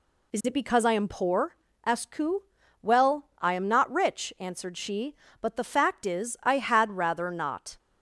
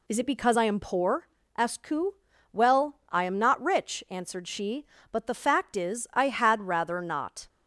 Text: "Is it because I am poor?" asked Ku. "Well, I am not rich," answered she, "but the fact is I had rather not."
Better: neither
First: none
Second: none

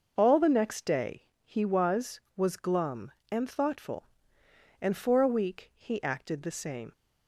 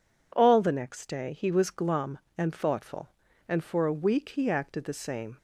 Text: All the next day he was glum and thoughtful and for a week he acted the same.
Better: second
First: starts louder than the rest; noticeable; until 1.1 s; 6 dB // says "was" twice; at 2.3 s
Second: none

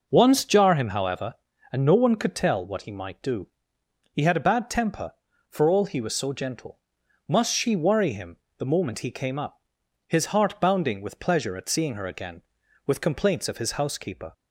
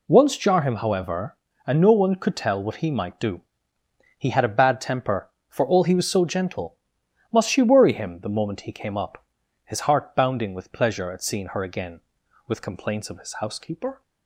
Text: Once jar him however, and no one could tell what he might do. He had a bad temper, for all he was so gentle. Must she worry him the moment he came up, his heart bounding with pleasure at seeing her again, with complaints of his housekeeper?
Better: second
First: starts louder than the rest; noticeable; until 1.3 s; 5.5 dB // pauses between "him" and "the"; slight; at 8.3 s; 0.20 s long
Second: none

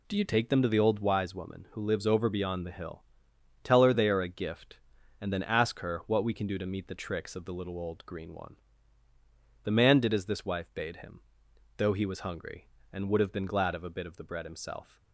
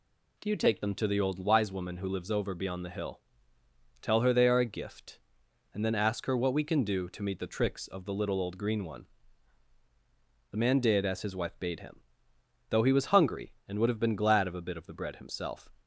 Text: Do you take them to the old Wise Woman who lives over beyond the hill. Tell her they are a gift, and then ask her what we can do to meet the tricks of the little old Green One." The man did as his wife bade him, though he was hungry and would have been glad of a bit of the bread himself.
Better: second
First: says "this" for "his"; at 10.2 s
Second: none

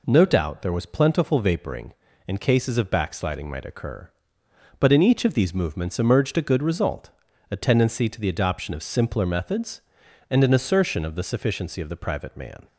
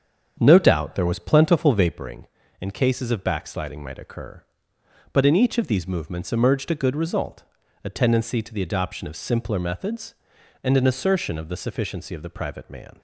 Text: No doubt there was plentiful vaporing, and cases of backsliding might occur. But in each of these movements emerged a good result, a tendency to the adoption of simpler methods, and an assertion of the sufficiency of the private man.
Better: first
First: none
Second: starts louder than the rest; strong; until 2.1 s; 7.5 dB

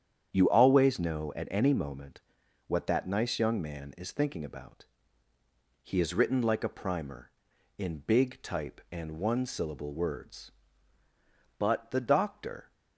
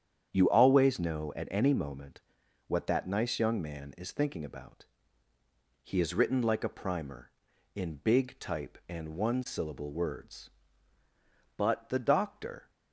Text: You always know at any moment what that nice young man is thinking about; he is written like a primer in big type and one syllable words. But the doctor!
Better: neither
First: starts louder than the rest; strong; until 1.3 s; 8.5 dB // pauses between "moment" and "what"; noticeable; at 2.2 s; 0.48 s long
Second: starts louder than the rest; strong; until 1.3 s; 8.5 dB // pauses between "moment" and "what"; noticeable; at 2.2 s; 0.48 s long

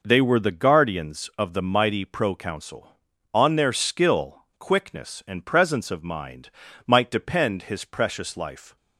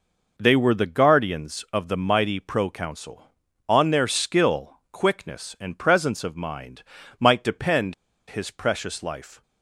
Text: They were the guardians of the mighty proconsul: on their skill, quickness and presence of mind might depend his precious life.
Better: first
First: pauses between "mind" and "might"; slight; at 6.4 s; 0.36 s long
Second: pauses between "mind" and "might"; slight; at 6.8 s; 0.36 s long // pauses between "depend" and "his"; slight; at 7.9 s; 0.35 s long

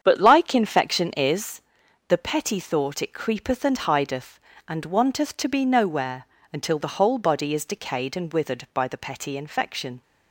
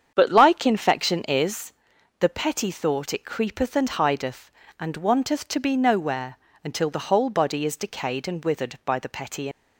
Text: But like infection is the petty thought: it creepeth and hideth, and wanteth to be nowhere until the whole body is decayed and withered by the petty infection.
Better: first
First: starts louder than the rest; strong; until 1.0 s; 8 dB // pauses between "is" and "the"; noticeable; at 1.6 s; 0.46 s long // pauses between "nowhere" and "until"; slight; at 6.2 s; 0.26 s long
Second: starts louder than the rest; strong; until 1.1 s; 8 dB // pauses between "is" and "the"; noticeable; at 1.7 s; 0.46 s long // pauses between "nowhere" and "until"; slight; at 6.3 s; 0.26 s long // stops before "infection"; at 9.5 s

